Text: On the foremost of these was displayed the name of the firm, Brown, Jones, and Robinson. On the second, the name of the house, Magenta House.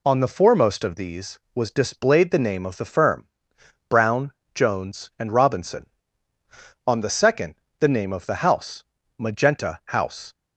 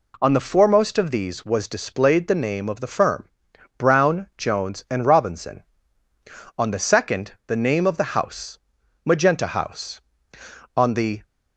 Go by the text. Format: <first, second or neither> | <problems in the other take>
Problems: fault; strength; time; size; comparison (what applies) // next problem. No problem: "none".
first | goes on to say "On the"; slight; from 10.7 s on; 0.48 s long